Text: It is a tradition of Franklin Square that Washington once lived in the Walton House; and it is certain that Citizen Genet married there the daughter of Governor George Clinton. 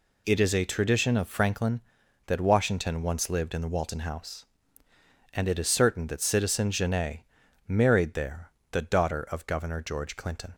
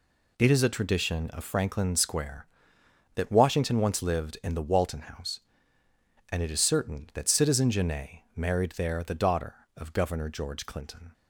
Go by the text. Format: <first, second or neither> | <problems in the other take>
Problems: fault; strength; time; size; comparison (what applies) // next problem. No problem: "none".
second | skips "Square"; at 2.0 s // pauses between "Genet" and "married"; noticeable; at 7.2 s; 0.48 s long; slight in the second // pauses between "there" and "the"; slight; at 8.4 s; 0.22 s long